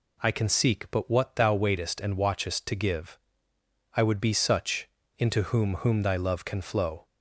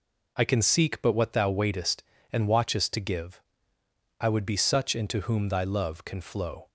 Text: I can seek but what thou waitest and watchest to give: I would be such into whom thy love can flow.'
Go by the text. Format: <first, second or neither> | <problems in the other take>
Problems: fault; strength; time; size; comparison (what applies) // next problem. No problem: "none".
second | pauses between "such" and "into"; slight; at 4.8 s; 0.28 s long // says "whom" twice; at 5.7 s